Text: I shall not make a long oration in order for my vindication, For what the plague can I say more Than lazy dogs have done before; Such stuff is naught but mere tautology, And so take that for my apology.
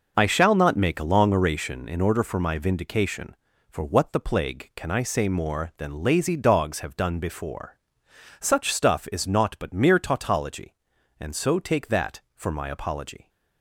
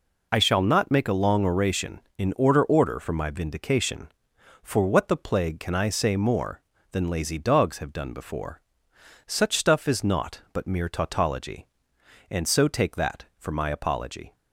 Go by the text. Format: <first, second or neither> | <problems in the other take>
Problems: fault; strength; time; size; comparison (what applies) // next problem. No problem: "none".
first | says "order" twice; at 2.6 s